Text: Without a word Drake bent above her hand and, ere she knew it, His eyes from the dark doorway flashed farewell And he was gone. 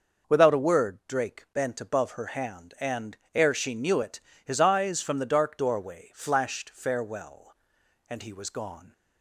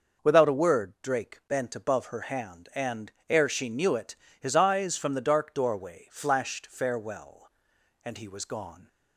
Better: neither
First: none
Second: none

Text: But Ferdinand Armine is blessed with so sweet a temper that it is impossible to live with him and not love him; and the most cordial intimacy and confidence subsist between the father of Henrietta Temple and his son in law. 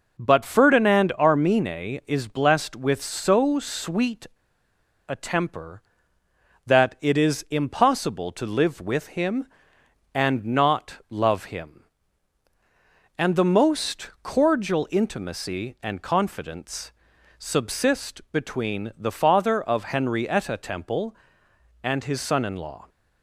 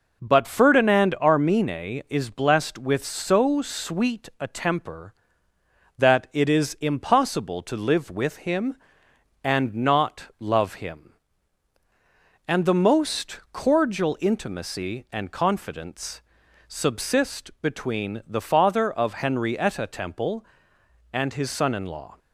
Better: second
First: pauses between "sweet" and "a"; noticeable; at 4.2 s; 0.81 s long // pauses between "confidence" and "subsist"; noticeable; at 16.9 s; 0.46 s long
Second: pauses between "confidence" and "subsist"; noticeable; at 16.2 s; 0.46 s long

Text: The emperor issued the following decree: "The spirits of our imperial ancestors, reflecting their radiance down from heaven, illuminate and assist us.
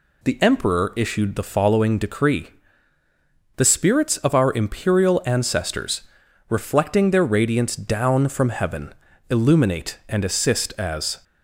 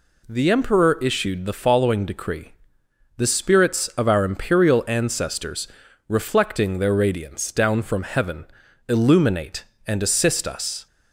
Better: second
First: says "as" for "us"; at 10.7 s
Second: none

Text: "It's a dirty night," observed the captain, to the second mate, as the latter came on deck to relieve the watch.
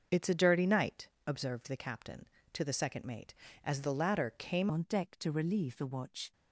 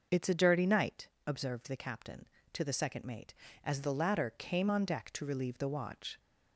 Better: second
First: starts louder than the rest; until 1.3 s; 6.5 dB // changes voice at "on"; from 4.7 s on; 1.6 s long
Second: none

